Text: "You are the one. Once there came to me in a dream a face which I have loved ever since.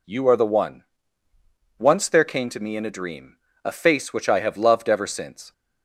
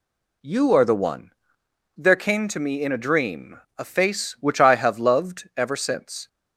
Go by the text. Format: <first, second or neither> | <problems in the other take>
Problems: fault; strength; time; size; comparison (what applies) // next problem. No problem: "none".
first | skips "Once"; at 1.6 s // pauses between "dream" and "a"; slight; at 3.5 s; 0.20 s long; slight in the first